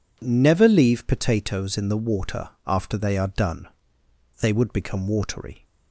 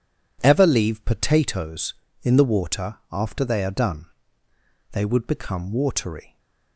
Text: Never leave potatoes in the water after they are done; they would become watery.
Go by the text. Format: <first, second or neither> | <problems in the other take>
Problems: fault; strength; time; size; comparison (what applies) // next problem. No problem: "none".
first | says "Ever" for "Never"; at 0.4 s // pauses between "water" and "after"; slight; at 2.9 s; 0.16 s long; slight in the first